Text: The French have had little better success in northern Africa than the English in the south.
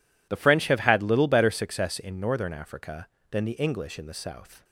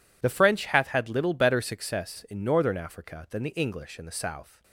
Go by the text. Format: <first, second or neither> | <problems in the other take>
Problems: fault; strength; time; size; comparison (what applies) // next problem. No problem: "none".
first | says "hath" for "have"; at 0.6 s